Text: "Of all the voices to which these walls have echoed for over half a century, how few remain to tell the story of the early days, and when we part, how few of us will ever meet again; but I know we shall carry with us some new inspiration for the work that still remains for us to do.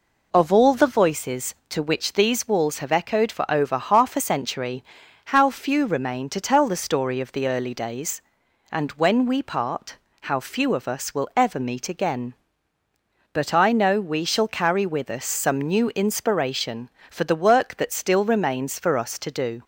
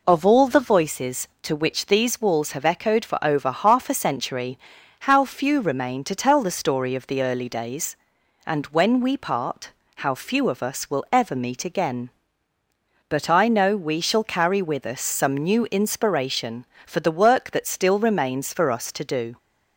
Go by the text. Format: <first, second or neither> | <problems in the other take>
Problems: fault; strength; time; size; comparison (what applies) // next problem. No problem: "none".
neither | none